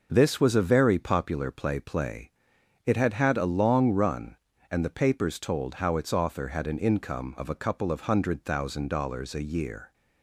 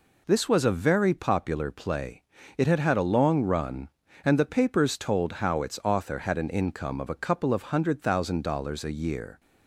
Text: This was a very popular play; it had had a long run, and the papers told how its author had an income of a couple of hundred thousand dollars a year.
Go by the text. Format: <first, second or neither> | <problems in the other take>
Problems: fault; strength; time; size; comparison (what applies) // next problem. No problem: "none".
second | says "play" twice; at 1.7 s